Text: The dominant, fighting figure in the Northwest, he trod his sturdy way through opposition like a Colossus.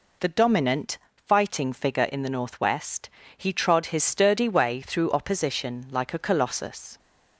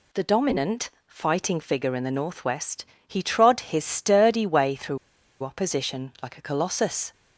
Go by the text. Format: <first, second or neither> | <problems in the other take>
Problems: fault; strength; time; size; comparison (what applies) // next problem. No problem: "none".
first | pauses between "through" and "opposition"; at 4.9 s; 0.44 s long